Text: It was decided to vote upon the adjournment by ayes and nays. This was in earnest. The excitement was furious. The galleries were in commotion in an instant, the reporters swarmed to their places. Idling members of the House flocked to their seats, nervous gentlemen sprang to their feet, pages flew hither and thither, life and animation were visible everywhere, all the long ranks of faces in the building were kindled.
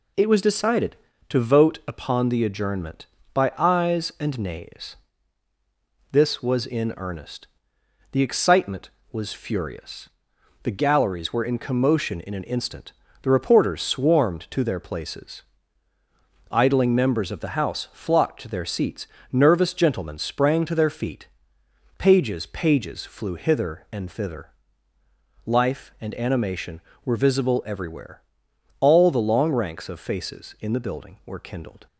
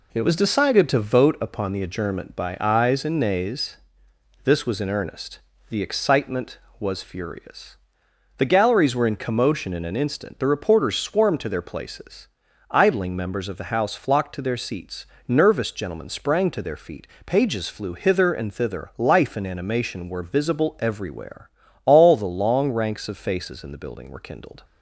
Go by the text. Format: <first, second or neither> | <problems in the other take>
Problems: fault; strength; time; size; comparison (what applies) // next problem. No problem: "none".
second | says "pages" twice; at 22.4 s